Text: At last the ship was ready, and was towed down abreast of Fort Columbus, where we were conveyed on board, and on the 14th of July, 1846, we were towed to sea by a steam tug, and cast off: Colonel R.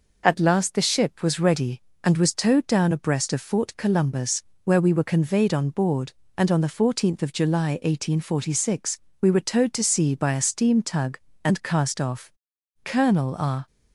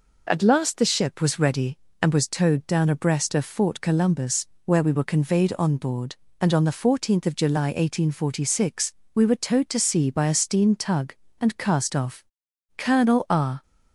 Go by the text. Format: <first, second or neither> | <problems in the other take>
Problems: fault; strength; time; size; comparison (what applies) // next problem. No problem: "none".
neither | none